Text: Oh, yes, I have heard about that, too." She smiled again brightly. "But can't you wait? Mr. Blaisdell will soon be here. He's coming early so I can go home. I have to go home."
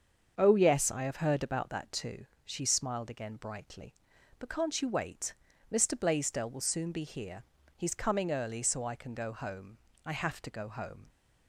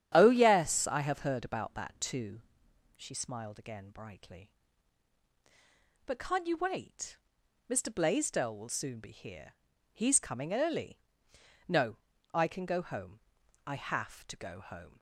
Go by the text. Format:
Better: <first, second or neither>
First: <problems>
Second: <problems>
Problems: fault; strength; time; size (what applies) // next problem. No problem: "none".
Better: first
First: starts louder than the rest; until 1.3 s; 7 dB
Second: starts louder than the rest; strong; until 1.1 s; 10 dB // says "no" for "so"; at 11.6 s